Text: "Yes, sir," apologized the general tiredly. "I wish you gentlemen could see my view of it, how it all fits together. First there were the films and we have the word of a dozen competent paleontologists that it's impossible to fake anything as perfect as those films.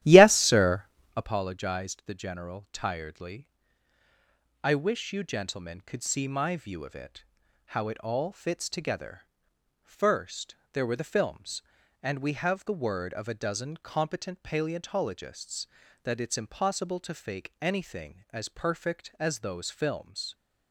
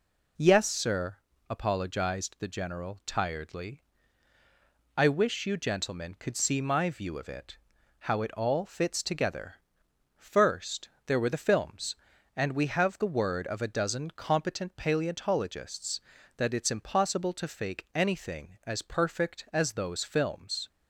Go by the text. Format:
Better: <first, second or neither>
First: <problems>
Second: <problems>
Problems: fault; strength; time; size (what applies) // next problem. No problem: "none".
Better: second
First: starts louder than the rest; strong; until 1.4 s; 13 dB // pauses between "First" and "there"; slight; at 10.5 s; 0.16 s long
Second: pauses between "First" and "there"; slight; at 10.8 s; 0.16 s long